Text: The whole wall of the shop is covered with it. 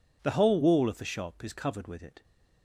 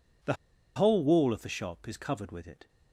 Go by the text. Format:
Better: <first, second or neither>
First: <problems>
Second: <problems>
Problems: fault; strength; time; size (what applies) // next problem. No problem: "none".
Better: first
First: none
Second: pauses between "The" and "whole"; at 0.3 s; 0.42 s long